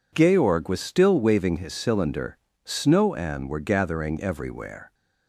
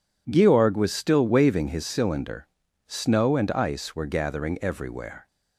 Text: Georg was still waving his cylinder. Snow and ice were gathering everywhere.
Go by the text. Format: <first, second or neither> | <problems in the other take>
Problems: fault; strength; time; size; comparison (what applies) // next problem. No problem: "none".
second | skips "ice"; at 3.4 s